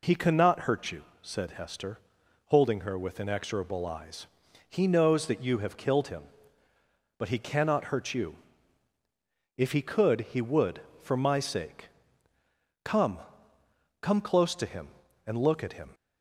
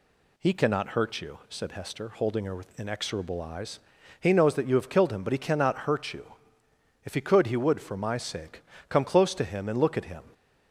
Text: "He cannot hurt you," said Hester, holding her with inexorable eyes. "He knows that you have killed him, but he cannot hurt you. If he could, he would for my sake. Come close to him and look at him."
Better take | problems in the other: second | says "Come" twice; at 14.0 s

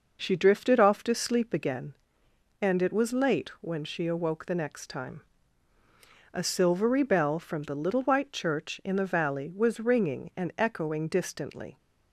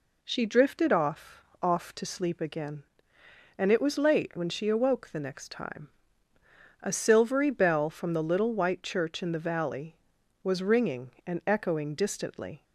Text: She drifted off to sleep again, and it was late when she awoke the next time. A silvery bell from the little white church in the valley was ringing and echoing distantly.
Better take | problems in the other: first | says "off" twice; at 1.6 s

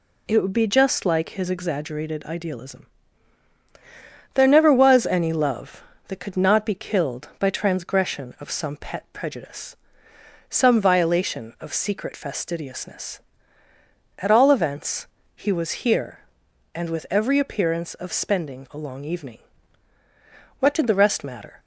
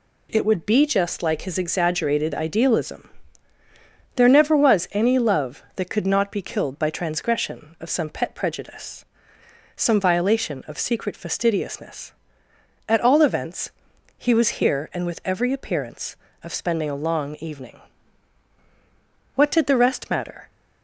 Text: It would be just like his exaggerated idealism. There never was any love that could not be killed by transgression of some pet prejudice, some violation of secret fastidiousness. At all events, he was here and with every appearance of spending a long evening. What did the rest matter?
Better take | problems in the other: neither | none

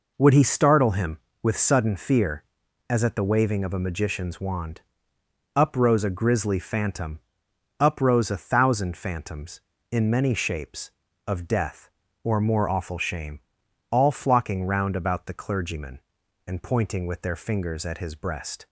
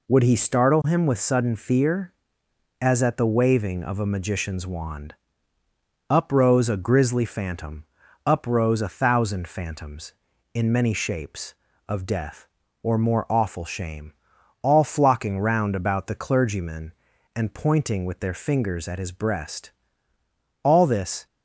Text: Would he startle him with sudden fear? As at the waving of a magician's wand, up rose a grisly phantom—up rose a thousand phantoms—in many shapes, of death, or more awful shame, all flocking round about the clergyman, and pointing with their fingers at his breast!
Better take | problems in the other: first | goes on to say "All this"; noticeable; from 20.6 s on; 0.64 s long

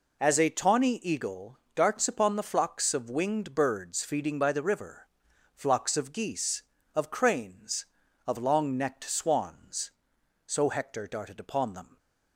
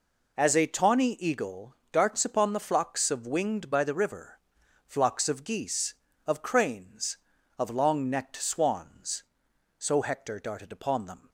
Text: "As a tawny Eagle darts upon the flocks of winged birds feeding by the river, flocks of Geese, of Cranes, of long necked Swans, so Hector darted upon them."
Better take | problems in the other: first | pauses between "Eagle" and "darts"; slight; at 1.7 s; 0.16 s long; slight in the first // skips "birds feeding"; at 3.7 s

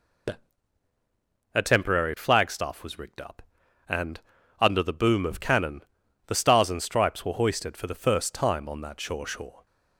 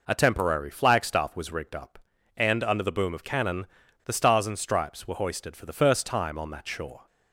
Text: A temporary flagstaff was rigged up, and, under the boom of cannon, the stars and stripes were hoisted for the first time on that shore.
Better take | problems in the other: second | says "shore" twice; at 9.2 s

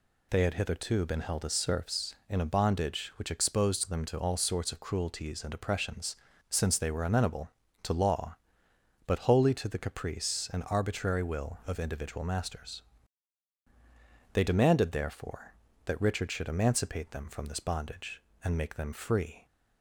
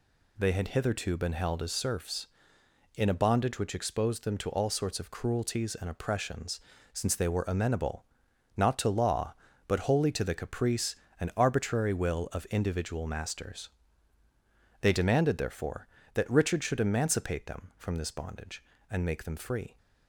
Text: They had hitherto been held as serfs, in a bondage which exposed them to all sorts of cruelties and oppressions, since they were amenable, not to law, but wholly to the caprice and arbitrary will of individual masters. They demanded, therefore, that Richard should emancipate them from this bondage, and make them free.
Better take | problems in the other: second | skips "not"; at 7.6 s

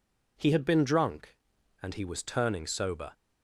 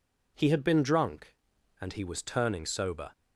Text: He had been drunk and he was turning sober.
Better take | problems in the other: neither | none

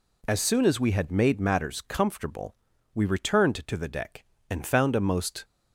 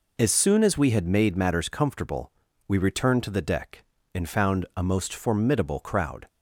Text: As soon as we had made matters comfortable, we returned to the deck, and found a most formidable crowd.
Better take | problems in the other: second | stops before "formidable crowd"; at 5.4 s

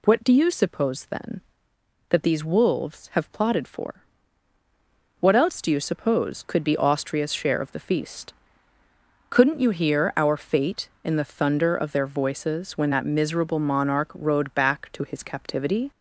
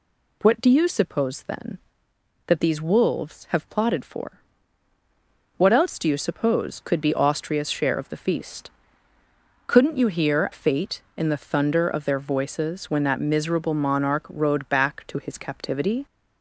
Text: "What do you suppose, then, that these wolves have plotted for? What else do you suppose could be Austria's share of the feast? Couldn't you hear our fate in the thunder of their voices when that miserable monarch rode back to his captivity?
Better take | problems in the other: first | skips "our"; at 10.5 s

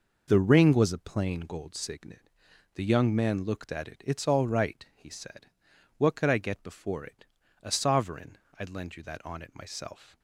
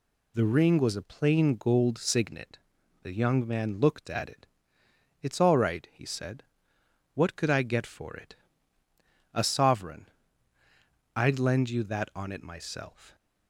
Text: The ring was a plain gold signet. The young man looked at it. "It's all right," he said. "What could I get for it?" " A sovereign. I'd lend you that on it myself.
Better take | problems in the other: second | says "before" for "for"; at 6.6 s

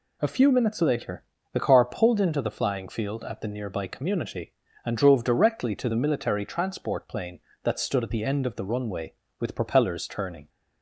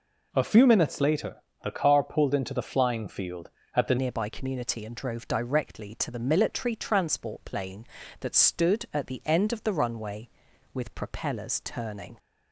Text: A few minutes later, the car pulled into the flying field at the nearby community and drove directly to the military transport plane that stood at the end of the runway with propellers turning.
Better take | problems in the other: first | changes voice at "nearby"; from 3.9 s on; 8.2 s long

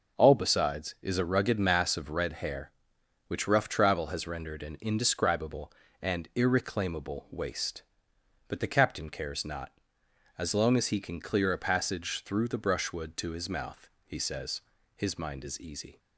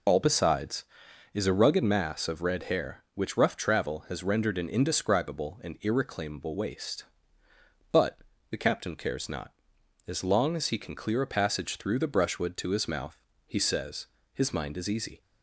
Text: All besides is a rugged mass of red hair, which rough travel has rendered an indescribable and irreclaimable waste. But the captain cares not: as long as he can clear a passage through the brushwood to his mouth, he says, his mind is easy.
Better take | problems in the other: first | loses the start of "All"; at 0.0 s; 40 ms // pauses between "But" and "the"; slight; at 8.1 s; 0.32 s long

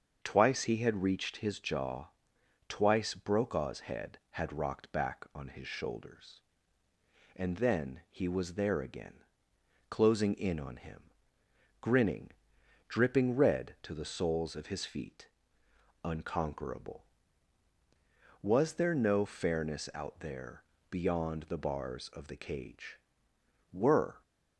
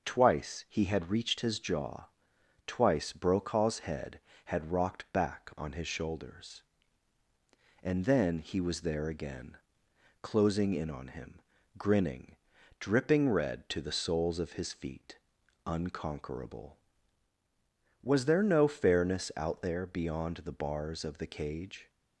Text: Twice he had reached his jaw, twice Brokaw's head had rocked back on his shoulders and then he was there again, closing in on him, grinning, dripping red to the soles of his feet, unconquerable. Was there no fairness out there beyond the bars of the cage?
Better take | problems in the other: second | starts louder than the rest; until 1.2 s; 7 dB; also in the second // pauses between "there" and "beyond"; slight; at 20.6 s; 0.28 s long // goes on to say "Were"; from 23.7 s on; 0.50 s long

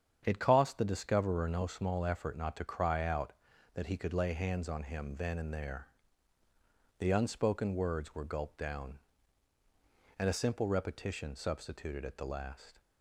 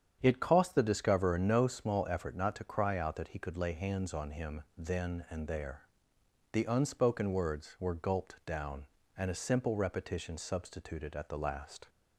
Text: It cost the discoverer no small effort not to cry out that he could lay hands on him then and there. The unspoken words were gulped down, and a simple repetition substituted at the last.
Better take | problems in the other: neither | starts louder than the rest; strong; the same in both

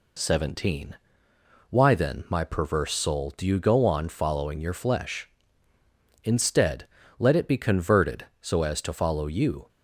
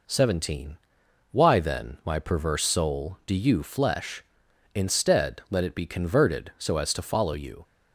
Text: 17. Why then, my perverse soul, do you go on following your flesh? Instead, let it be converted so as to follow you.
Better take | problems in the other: first | skips "go on following your"; at 3.6 s

